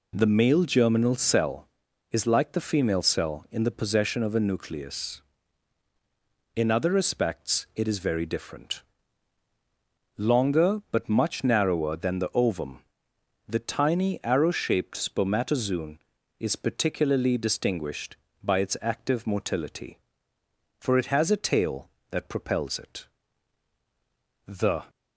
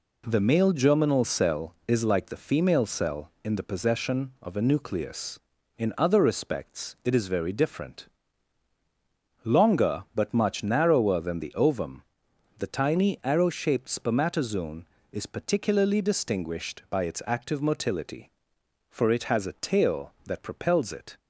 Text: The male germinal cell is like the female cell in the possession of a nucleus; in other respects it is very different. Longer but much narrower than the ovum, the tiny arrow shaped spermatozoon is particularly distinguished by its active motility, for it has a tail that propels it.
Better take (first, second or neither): second